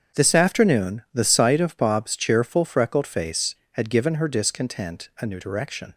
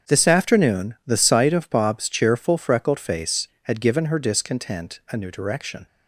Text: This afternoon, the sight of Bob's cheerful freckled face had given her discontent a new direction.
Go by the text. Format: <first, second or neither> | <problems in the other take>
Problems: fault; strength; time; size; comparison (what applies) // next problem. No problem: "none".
neither | starts louder than the rest; strong; the same in both